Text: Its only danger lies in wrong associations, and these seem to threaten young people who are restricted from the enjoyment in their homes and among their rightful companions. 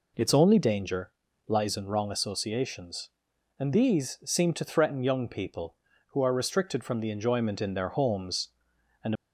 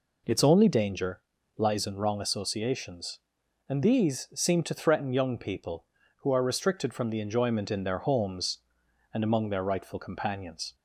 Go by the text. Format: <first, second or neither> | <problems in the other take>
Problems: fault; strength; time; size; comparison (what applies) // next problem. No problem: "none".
second | pauses between "danger" and "lies"; slight; at 1.1 s; 0.36 s long; slight in the second // stops before "among their rightful companions"; at 9.1 s